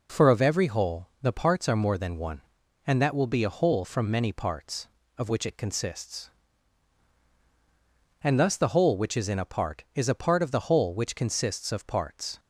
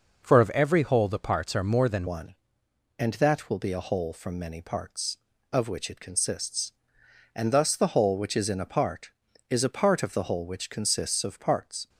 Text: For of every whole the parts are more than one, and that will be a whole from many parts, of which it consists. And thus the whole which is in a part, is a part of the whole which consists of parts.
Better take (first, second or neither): first